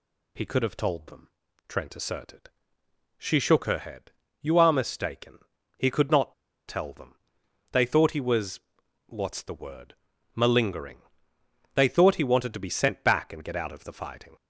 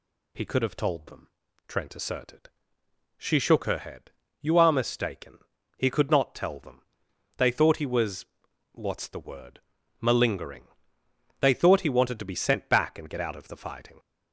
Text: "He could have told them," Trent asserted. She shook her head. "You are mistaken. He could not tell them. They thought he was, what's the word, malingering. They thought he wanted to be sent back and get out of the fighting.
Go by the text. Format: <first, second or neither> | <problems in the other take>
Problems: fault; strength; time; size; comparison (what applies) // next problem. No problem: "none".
second | pauses between "not" and "tell"; slight; at 6.3 s; 0.33 s long